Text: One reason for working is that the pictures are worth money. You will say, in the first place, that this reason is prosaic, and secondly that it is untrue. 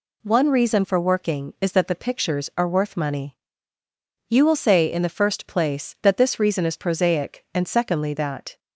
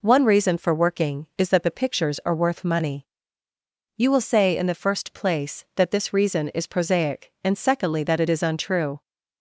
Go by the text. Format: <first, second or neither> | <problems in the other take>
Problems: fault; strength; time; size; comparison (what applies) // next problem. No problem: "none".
second | stops before "it is untrue"; at 8.5 s